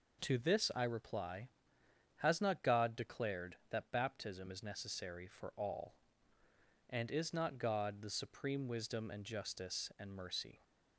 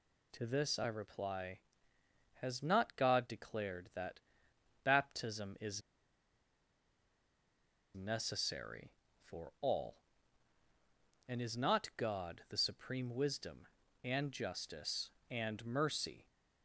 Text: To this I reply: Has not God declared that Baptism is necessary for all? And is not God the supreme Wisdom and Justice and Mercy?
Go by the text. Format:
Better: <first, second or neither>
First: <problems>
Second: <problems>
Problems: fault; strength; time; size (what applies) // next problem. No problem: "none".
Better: first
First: none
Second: pauses between "that" and "Baptism"; noticeable; at 4.1 s; 0.62 s long // pauses between "is" and "necessary"; strong; at 5.8 s; 2.1 s long